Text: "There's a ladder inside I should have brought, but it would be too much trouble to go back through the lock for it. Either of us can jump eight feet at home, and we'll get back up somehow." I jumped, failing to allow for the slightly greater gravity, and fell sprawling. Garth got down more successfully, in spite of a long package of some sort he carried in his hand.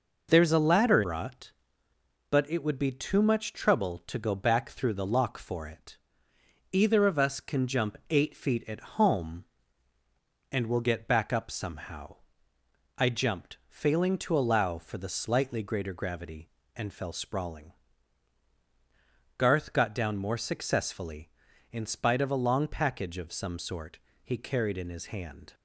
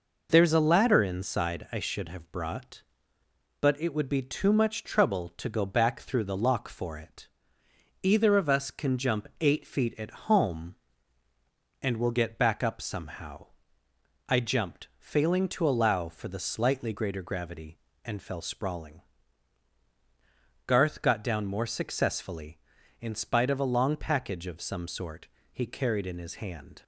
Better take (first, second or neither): second